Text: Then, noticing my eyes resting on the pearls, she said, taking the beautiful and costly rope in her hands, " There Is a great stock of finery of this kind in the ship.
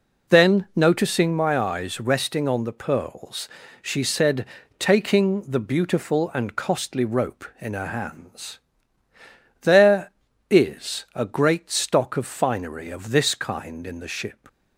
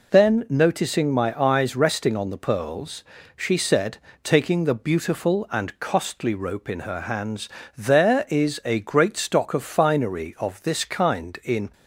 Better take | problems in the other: first | stops before "the ship"; at 11.7 s

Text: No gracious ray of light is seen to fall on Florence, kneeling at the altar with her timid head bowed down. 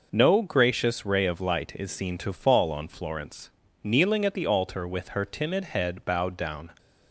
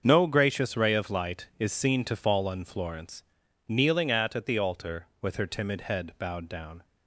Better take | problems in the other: first | starts louder than the rest; until 1.0 s; 6.5 dB // says "at" twice; at 4.3 s

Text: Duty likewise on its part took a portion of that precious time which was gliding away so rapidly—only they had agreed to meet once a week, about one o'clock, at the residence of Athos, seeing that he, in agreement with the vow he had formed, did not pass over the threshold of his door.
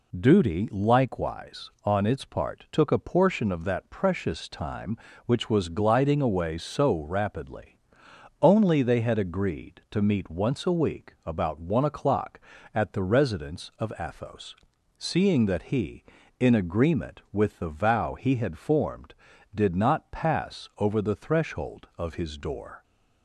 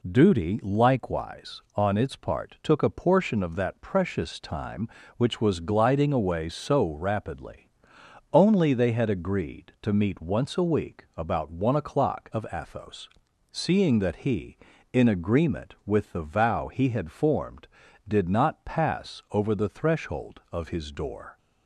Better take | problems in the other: first | skips "at the residence"; at 12.3 s

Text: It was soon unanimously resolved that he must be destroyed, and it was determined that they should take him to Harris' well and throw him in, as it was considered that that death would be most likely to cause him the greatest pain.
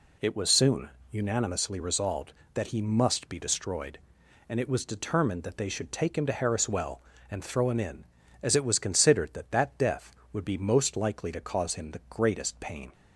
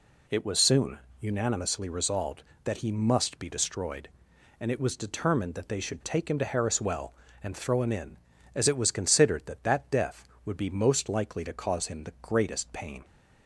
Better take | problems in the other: neither | pauses between "soon" and "unanimously"; slight; the same in both

